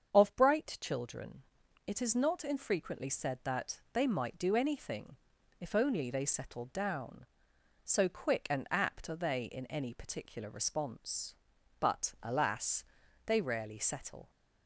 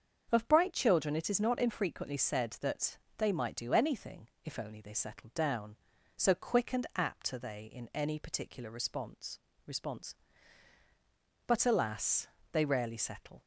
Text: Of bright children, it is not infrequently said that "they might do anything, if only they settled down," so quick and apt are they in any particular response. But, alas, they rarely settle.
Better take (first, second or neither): first